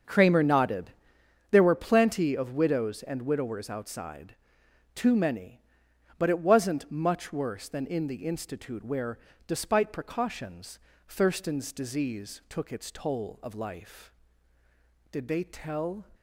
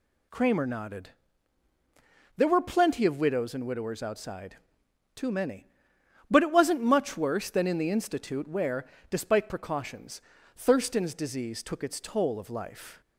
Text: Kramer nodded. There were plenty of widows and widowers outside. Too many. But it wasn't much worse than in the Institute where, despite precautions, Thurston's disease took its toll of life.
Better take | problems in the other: second | starts louder than the rest; until 1.6 s; 7 dB // goes on to say "Did they tell"; noticeable; from 15.1 s on; 0.94 s long

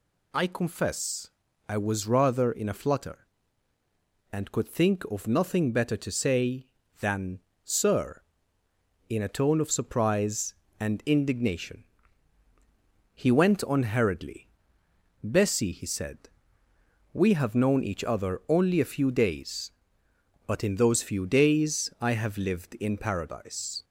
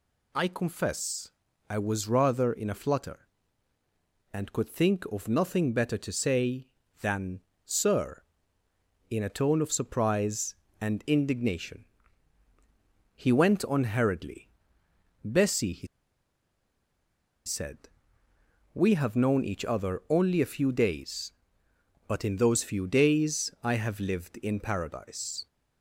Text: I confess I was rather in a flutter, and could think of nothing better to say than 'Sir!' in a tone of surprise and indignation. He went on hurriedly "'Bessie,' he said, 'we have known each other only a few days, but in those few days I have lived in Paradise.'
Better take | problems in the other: first | pauses between "confess" and "I"; at 1.3 s; 0.40 s long; also in the first // pauses between "than" and "Sir"; slight; at 7.3 s; 0.26 s long; slight in the first // pauses between "hurriedly" and "Bessie"; noticeable; at 14.5 s; 0.72 s long; noticeable in the first // pauses between "he" and "said"; strong; at 15.8 s; 1.5 s long

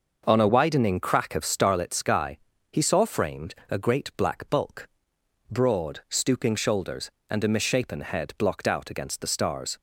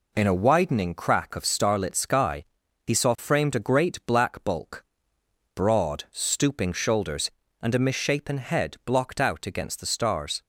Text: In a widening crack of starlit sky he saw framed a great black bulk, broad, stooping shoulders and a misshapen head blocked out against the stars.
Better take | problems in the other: second | starts louder than the rest; noticeable; until 1.2 s; 6 dB // says "On" for "In"; at 0.2 s // pauses between "sky" and "he"; slight; at 2.3 s; 0.34 s long; also in the second

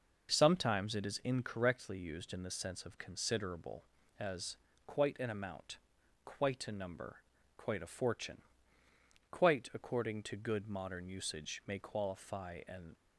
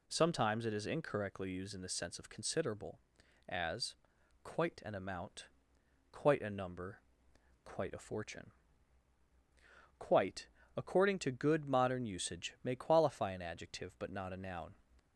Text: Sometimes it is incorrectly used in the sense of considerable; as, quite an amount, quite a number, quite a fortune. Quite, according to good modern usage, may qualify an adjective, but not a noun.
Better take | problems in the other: second | stops before "adjective but not a noun"; at 12.9 s

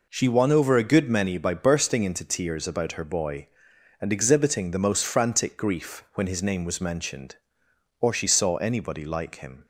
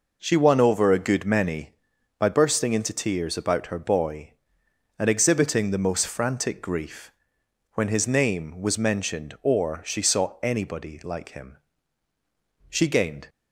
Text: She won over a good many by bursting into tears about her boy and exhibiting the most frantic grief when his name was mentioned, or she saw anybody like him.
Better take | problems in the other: first | pauses between "grief" and "when"; noticeable; at 7.0 s; 0.66 s long // goes on to say "She gained"; from 12.6 s on; 0.60 s long

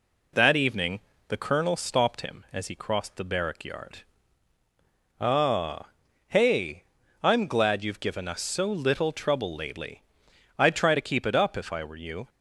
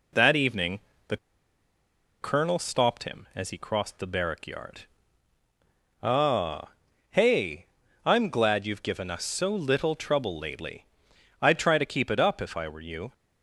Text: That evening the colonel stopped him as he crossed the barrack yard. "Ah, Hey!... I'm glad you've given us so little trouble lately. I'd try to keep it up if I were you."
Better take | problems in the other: first | pauses between "evening" and "the"; slight; at 0.7 s; 0.28 s long; slight in the first // pauses between "the" and "colonel"; at 1.1 s; 1.0 s long

